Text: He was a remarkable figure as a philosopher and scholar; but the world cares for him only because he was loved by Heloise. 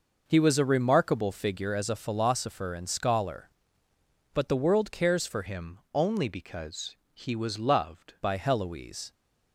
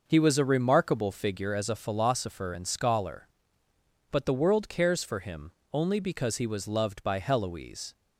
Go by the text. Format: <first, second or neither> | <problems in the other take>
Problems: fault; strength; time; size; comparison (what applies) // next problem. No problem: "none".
second | changes voice from "him" to "loved"; from 5.4 to 8.1 s; 2.7 s long // pauses between "him" and "only"; slight; at 5.7 s; 0.16 s long; slight in the second // pauses between "because" and "he"; slight; at 6.9 s; 0.16 s long